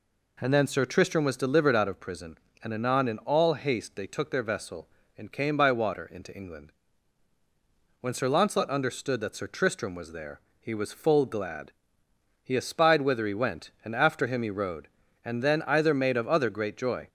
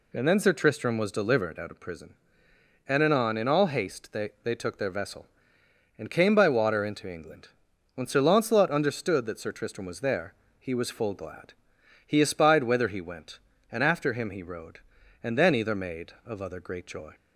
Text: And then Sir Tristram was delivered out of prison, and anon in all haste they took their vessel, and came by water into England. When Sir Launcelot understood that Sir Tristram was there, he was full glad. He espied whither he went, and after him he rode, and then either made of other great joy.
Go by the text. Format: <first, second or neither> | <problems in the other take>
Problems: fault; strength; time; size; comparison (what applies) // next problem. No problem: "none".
first | says "they" twice; at 4.4 s